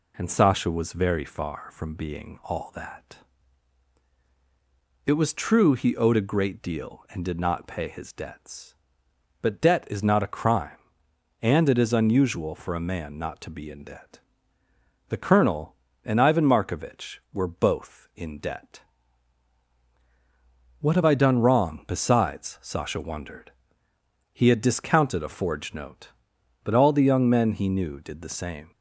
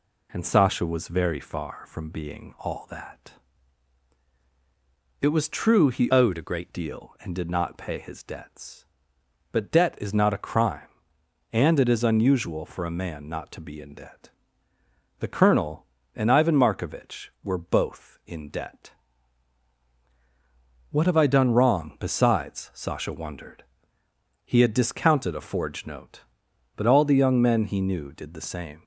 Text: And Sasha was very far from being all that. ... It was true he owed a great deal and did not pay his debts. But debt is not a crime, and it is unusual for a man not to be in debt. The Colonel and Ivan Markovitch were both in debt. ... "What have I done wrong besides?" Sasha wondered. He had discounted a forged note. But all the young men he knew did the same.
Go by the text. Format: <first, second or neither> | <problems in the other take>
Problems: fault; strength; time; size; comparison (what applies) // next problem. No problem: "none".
first | changes voice from "owed" to "great"; from 6.0 to 6.6 s; 0.6 s long